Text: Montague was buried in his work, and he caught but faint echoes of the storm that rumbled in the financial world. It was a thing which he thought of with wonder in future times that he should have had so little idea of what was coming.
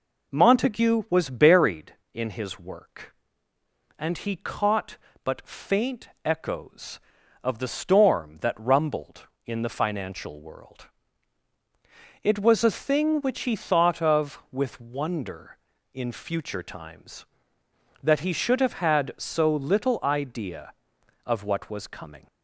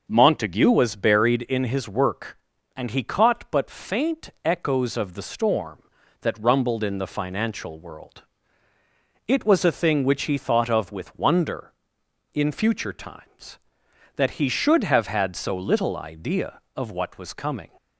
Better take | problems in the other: neither | pauses between "faint" and "echoes"; slight; the same in both

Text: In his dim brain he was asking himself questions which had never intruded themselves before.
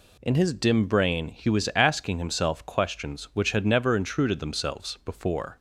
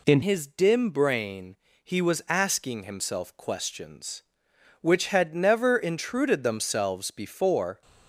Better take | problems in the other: first | changes voice at "his"; from 0.2 s on; 7.6 s long // pauses between "brain" and "he"; slight; at 1.5 s; 0.26 s long

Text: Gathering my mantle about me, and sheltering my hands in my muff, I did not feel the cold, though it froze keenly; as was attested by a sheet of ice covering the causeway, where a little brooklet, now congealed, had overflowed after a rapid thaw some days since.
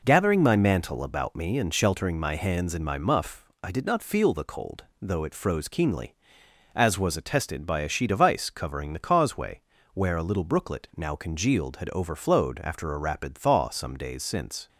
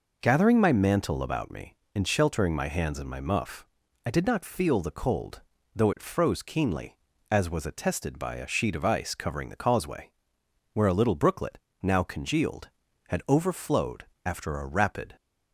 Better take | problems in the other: first | pauses between "overflowed" and "after"; slight; at 14.0 s; 0.22 s long // stops before "thaw some days since"; at 15.1 s

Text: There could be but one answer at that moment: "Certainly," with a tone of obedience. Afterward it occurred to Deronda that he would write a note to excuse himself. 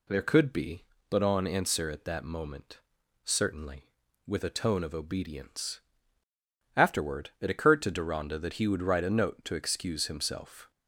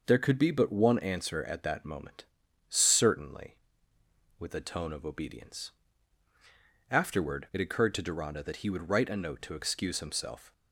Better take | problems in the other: second | says "on" for "one"; at 1.2 s

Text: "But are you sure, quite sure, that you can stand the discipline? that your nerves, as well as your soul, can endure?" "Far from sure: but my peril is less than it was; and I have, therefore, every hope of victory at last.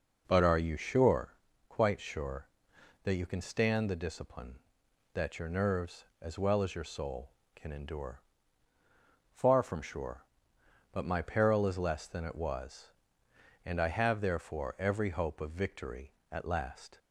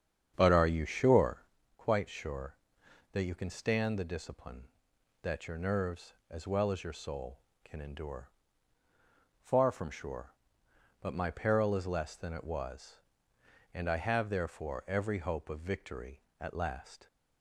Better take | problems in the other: first | starts louder than the rest; strong; until 1.5 s; 8.5 dB

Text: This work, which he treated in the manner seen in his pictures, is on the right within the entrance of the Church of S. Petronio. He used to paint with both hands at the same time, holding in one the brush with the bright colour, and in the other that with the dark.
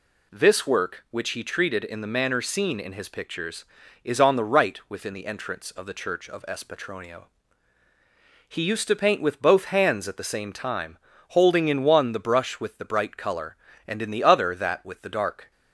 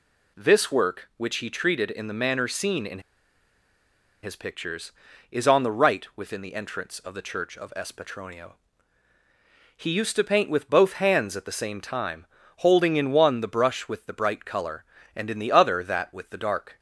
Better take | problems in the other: first | pauses between "in" and "his"; at 2.9 s; 1.2 s long

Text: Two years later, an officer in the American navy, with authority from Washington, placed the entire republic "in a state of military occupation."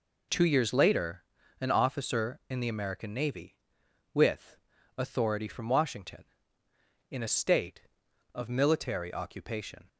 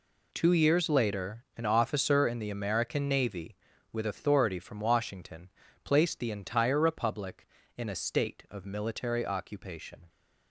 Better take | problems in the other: second | pauses between "with" and "authority"; at 4.5 s; 0.40 s long // skips "placed the entire republic"; at 6.6 s

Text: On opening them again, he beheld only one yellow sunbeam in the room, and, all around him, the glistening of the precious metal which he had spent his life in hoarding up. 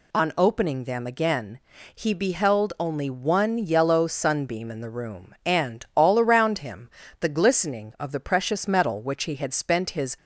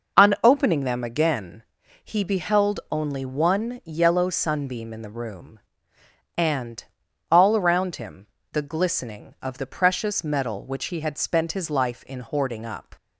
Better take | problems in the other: second | stops before "life in hoarding up"; at 10.1 s

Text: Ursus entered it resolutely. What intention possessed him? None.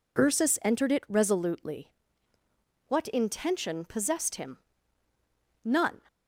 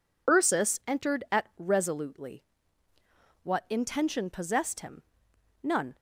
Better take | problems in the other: first | says "at" for "it"; at 1.3 s

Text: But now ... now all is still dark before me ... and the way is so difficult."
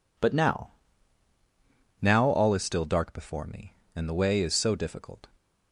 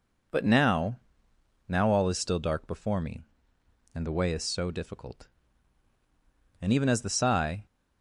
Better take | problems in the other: first | goes on to say "And even as the sigh"; noticeable; from 6.5 s on; 1.0 s long

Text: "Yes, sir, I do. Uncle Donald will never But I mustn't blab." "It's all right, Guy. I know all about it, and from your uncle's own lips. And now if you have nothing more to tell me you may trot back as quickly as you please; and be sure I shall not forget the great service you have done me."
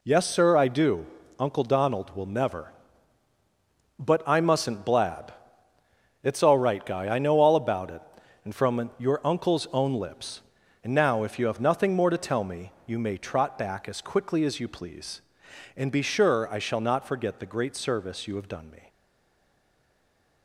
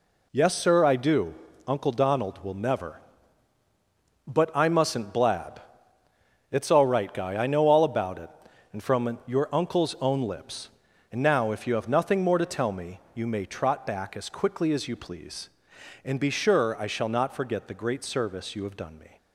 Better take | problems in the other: second | stays silent after the last word; noticeable; from 18.8 s on; 1.6 s long

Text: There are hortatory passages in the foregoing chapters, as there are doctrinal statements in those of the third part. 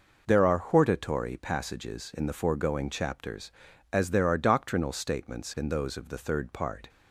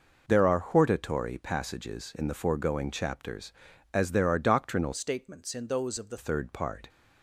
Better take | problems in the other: first | changes voice from "statements" to "the"; from 4.9 to 6.1 s; 1.2 s long

